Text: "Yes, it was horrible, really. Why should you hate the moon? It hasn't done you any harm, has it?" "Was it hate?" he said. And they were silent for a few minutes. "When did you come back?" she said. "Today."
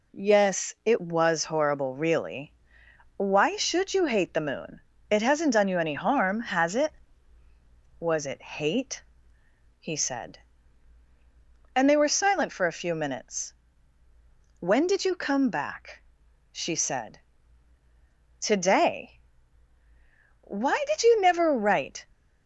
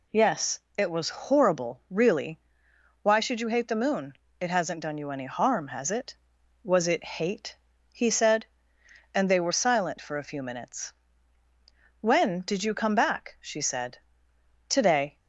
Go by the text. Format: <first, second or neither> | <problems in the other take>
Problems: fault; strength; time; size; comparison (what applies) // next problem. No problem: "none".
second | goes on to say "Why did you never write"; from 20.4 s on; 1.6 s long